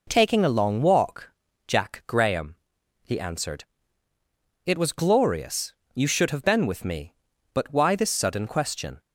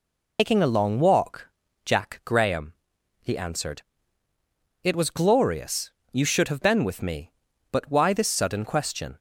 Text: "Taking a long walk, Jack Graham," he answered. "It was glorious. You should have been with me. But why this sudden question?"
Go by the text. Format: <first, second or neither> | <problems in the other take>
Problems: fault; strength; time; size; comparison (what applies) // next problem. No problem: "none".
first | loses the start of "Taking"; at 0.3 s; 145 ms